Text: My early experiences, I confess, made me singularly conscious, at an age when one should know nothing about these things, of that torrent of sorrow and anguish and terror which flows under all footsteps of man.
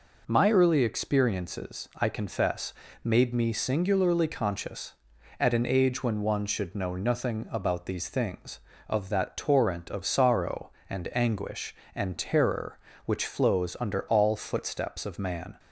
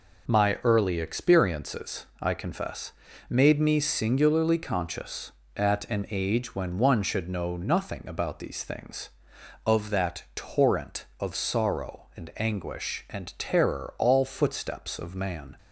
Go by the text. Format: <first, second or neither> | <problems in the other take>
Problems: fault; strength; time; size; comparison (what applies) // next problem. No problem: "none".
first | skips "which flows under"; at 13.9 s